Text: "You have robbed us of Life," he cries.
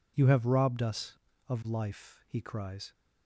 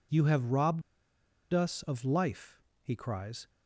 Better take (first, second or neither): first